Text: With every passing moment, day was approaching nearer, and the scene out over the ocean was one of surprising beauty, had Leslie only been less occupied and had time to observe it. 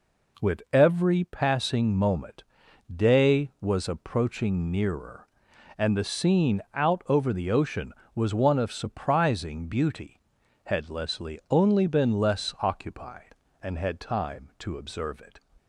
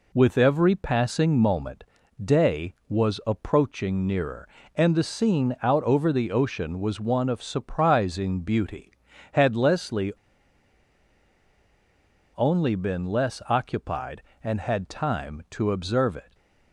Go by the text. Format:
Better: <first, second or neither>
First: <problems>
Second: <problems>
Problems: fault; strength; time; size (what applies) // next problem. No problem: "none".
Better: first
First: none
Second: pauses between "Leslie" and "only"; strong; at 10.1 s; 2.2 s long // stays silent after the last word; slight; from 16.2 s on; 0.5 s long